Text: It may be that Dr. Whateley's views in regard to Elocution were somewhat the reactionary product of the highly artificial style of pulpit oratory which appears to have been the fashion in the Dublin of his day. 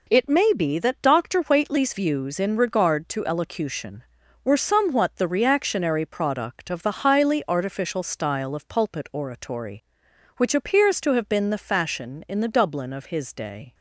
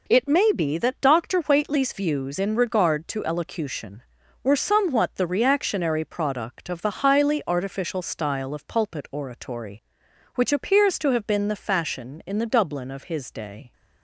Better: neither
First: none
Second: none

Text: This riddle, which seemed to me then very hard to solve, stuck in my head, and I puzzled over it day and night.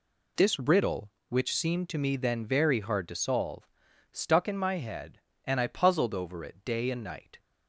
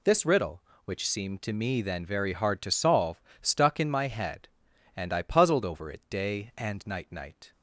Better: first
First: none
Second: says "night" twice; at 7.1 s

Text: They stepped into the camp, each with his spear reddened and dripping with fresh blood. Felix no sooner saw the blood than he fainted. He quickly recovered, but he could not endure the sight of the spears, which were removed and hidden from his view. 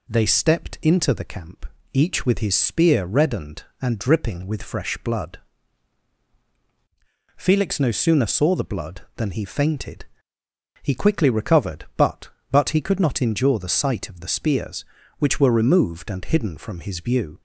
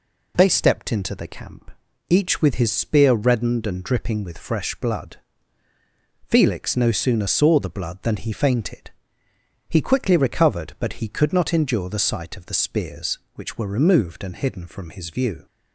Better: second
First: says "but" twice; at 12.4 s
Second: none

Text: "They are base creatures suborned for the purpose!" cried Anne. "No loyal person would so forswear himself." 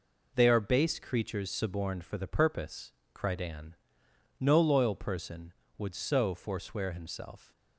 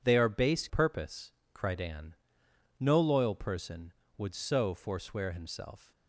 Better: first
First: none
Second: skips "creatures suborned for the"; at 0.6 s

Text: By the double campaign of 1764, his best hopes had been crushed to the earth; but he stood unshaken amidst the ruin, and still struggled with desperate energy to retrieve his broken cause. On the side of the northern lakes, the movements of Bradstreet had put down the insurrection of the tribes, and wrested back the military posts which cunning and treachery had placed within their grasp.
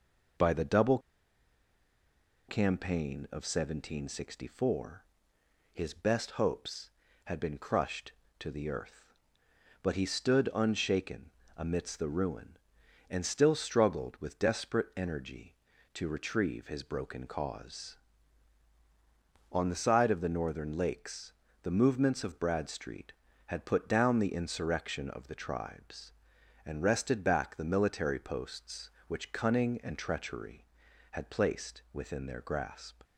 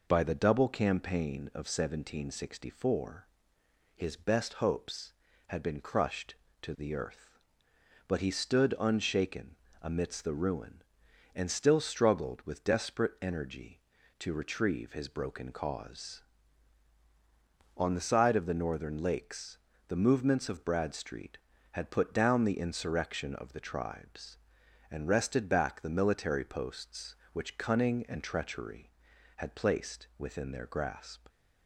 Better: second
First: pauses between "double" and "campaign"; strong; at 0.9 s; 1.4 s long // pauses between "unshaken" and "amidst"; slight; at 11.3 s; 0.28 s long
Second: pauses between "unshaken" and "amidst"; slight; at 9.5 s; 0.28 s long

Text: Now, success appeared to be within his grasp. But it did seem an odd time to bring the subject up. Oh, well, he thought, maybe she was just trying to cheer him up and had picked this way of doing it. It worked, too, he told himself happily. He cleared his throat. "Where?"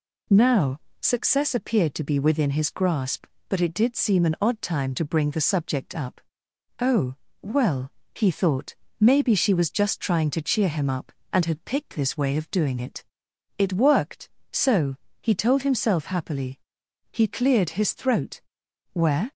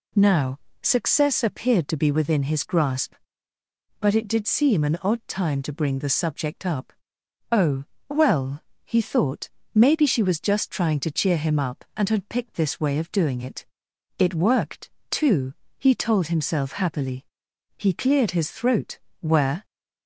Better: second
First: says "so" for "too"; at 14.5 s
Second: none

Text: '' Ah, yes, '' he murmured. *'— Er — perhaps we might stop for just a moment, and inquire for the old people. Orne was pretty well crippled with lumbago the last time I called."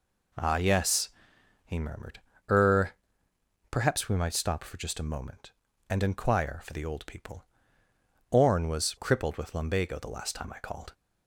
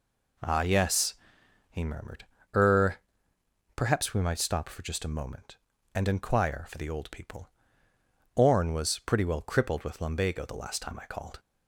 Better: second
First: skips "pretty well"; at 8.9 s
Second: none

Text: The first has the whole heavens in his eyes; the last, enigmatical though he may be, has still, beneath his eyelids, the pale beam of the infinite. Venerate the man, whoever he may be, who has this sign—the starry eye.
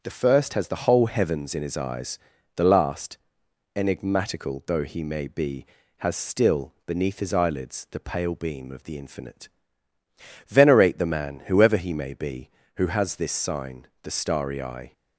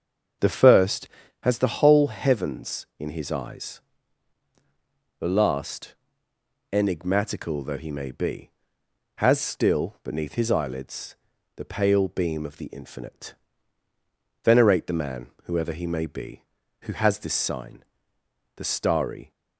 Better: first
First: starts louder than the rest; strong; until 1.0 s; 7 dB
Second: starts louder than the rest; until 1.7 s; 6.5 dB // stops before "eye"; at 19.3 s

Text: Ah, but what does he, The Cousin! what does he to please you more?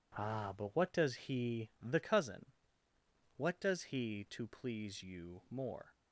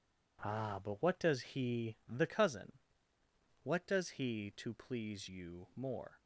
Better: neither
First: none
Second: none

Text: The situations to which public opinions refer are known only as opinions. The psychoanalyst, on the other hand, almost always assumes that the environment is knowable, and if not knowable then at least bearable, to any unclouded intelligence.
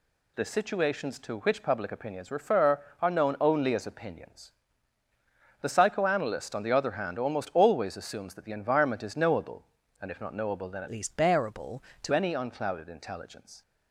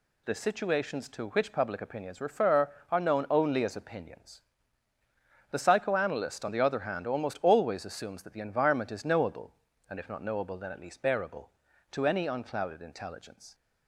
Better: second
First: changes voice from "least" to "to"; from 10.9 to 12.1 s; 1.2 s long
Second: none

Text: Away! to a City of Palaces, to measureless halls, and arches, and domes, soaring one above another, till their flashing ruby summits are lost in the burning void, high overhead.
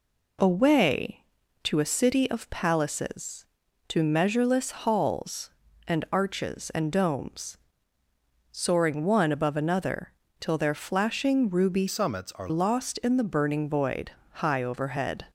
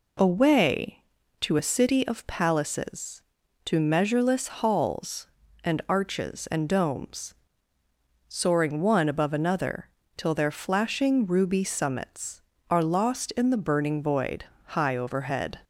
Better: second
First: changes voice from "summits" to "are"; from 11.8 to 12.4 s; 0.6 s long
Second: none

